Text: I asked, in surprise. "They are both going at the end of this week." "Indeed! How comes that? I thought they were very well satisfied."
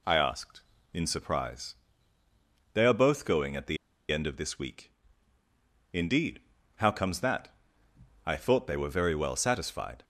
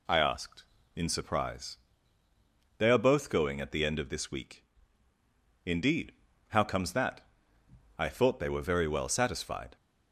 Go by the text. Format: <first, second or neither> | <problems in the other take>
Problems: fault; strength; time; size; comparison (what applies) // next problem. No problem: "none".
second | pauses between "the" and "end"; slight; at 3.7 s; 0.34 s long